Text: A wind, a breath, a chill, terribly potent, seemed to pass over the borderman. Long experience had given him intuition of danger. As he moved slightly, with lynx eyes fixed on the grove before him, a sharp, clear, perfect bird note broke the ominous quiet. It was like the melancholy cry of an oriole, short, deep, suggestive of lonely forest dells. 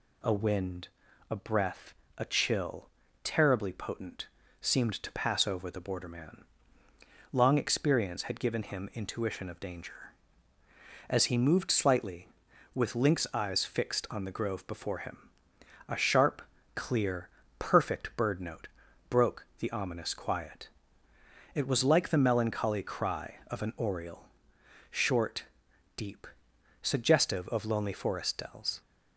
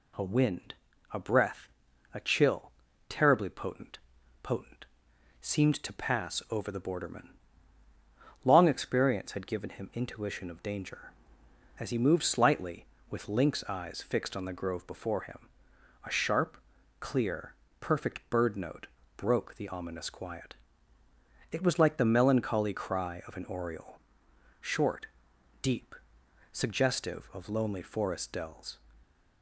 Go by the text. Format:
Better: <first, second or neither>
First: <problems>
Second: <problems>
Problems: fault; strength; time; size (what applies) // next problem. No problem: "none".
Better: first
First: pauses between "note" and "broke"; at 18.6 s; 0.40 s long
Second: says "potent" twice; at 4.4 s // pauses between "note" and "broke"; slight; at 18.8 s; 0.30 s long